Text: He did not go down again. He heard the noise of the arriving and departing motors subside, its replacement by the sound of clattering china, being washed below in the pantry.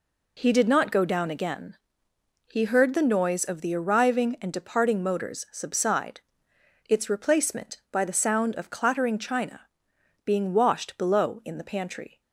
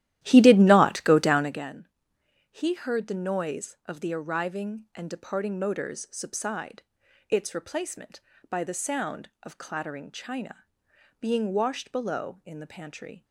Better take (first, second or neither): first